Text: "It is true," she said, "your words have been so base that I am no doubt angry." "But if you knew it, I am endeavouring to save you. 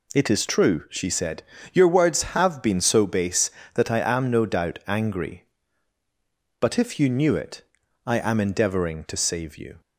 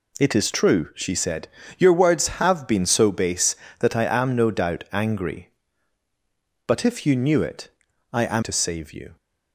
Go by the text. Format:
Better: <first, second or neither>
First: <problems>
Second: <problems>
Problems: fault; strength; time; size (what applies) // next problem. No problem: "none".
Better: first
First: none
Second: skips "endeavouring"; at 8.4 s